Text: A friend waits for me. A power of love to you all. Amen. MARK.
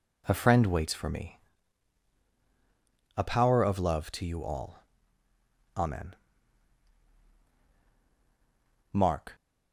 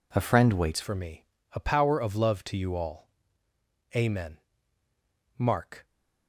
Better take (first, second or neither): first